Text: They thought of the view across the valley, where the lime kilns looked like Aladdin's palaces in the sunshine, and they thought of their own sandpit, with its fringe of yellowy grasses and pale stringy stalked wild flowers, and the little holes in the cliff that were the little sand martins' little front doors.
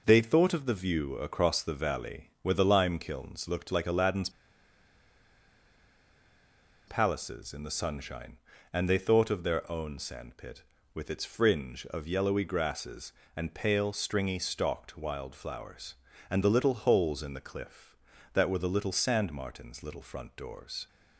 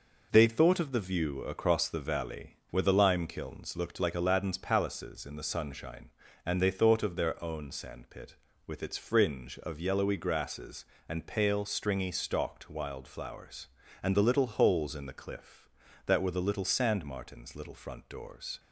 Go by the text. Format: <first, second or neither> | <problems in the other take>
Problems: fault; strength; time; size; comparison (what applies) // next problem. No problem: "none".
second | pauses between "Aladdin's" and "palaces"; strong; at 4.2 s; 2.5 s long